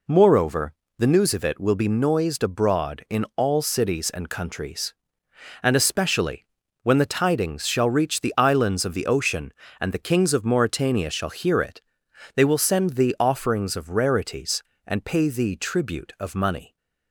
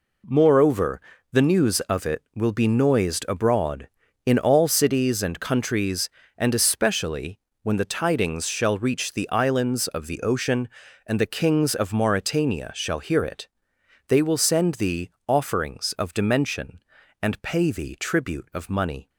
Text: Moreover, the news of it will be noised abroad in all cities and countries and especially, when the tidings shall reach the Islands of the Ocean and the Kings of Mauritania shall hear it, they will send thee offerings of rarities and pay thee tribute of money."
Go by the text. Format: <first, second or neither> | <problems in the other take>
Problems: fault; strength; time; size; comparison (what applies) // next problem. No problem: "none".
first | pauses between "thee" and "offerings"; slight; at 15.0 s; 0.18 s long // says "dimension" for "rarities"; at 16.1 s